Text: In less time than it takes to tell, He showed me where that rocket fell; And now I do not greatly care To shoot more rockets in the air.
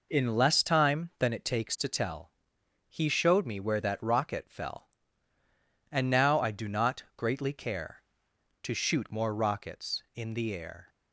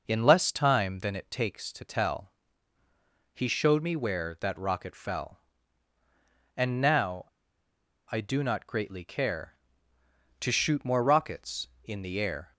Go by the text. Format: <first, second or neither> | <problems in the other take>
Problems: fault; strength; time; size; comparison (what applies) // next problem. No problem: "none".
first | pauses between "now" and "I"; noticeable; at 7.2 s; 0.85 s long